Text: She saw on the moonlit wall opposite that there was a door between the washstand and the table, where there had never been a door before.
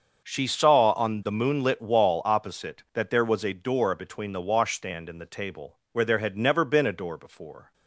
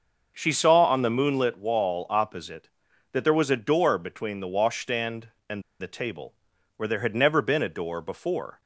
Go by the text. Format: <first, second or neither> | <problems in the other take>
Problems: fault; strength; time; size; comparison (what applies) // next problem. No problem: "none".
first | starts louder than the rest; until 1.3 s; 6.5 dB; also in the first // pauses between "and" and "the"; slight; at 5.6 s; 0.18 s long